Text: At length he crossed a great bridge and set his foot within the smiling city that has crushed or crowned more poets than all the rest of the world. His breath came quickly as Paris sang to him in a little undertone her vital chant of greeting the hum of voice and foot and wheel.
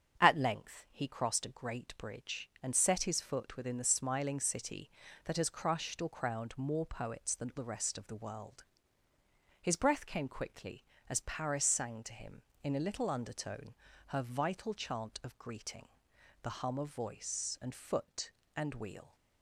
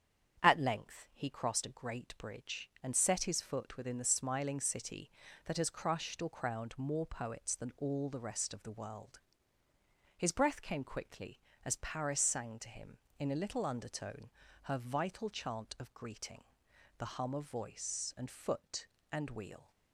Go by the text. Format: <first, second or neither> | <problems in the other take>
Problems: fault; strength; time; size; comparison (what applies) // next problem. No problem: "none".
second | starts louder than the rest; strong; until 1.2 s; 8.5 dB; strong in the second // skips "all"; at 7.5 s // pauses between "undertone" and "her"; slight; at 13.7 s; 0.34 s long; slight in the second // pauses between "greeting" and "the"; noticeable; at 15.8 s; 0.56 s long; noticeable in the second